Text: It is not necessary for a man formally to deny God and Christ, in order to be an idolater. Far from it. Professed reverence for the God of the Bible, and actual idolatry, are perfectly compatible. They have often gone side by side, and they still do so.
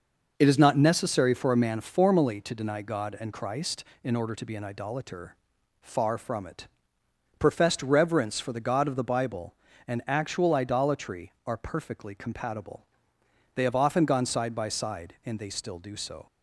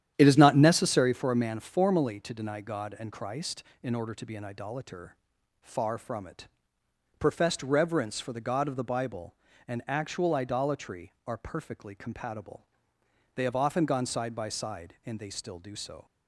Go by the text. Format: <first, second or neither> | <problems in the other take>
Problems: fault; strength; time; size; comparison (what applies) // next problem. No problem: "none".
first | starts louder than the rest; strong; until 1.1 s; 10.5 dB